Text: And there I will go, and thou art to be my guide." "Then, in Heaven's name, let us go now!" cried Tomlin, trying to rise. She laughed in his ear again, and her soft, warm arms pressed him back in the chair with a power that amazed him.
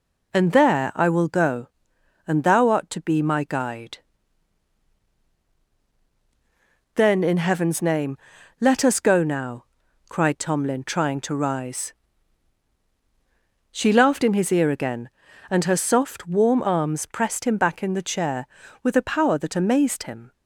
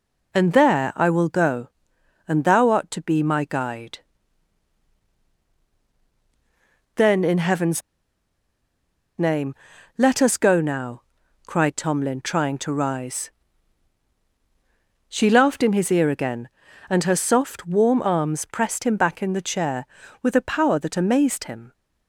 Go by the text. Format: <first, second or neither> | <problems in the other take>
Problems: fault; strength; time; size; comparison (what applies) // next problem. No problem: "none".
first | pauses between "Heaven's" and "name"; strong; at 7.8 s; 1.3 s long